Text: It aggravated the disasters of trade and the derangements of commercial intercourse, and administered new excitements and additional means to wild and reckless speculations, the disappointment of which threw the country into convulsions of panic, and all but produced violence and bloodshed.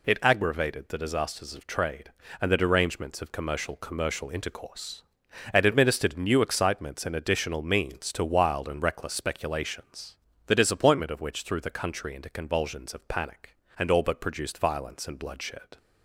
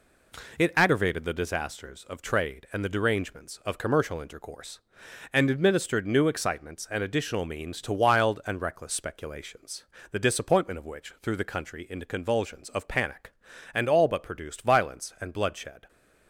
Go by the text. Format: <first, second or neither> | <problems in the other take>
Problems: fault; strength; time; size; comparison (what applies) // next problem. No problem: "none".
second | says "commercial" twice; at 3.7 s